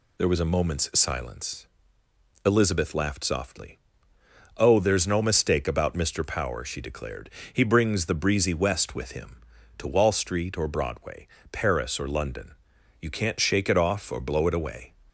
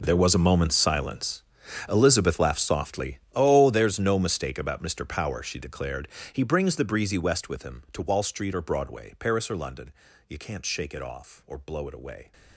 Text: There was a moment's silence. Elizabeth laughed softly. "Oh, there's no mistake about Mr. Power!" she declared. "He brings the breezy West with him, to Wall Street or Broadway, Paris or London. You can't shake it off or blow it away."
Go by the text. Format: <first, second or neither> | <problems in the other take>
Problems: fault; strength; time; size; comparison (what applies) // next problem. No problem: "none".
first | gets quieter; strong; throughout; 17 dB